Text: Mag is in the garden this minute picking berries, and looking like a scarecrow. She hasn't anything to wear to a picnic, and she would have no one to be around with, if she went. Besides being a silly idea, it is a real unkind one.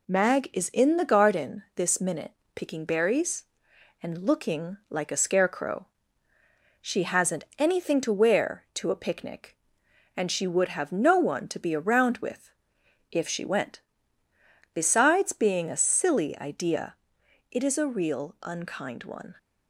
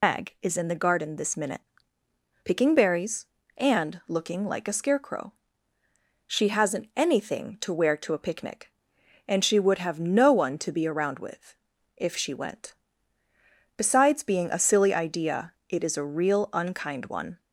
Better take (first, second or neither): first